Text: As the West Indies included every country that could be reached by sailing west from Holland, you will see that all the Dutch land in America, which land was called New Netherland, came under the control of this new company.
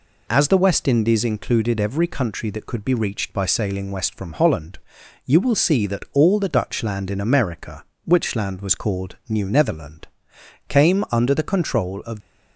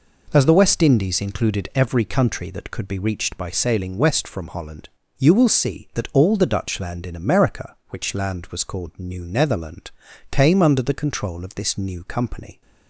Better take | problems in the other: second | stops before "this new company"; at 12.2 s

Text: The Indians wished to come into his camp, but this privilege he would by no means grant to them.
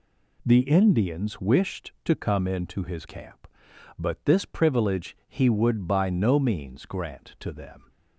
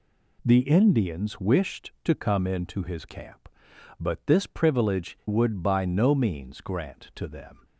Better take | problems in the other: first | skips "he"; at 5.2 s

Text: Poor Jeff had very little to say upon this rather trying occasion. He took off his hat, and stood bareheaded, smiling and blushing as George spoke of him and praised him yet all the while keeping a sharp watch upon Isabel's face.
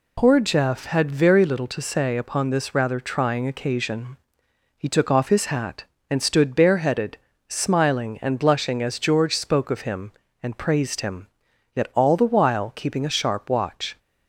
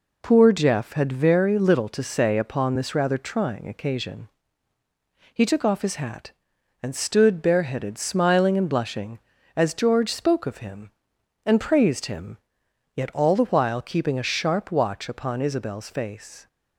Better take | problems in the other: second | pauses between "him" and "yet"; noticeable; at 11.2 s; 0.48 s long; noticeable in the second // stops before "upon Isabel's face"; at 13.9 s

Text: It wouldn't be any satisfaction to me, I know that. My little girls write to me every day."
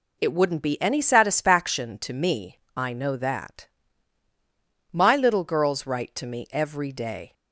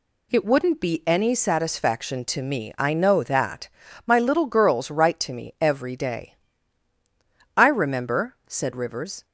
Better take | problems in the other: first | goes on to say "I remember said Rivers"; strong; from 7.5 s on; 1.6 s long

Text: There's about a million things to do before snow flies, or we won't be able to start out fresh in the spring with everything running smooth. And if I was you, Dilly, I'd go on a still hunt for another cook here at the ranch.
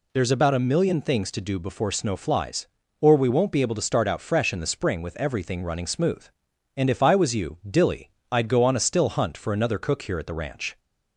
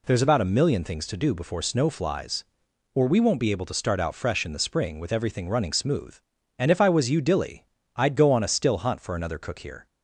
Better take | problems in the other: first | stops before "at the ranch"; at 9.8 s

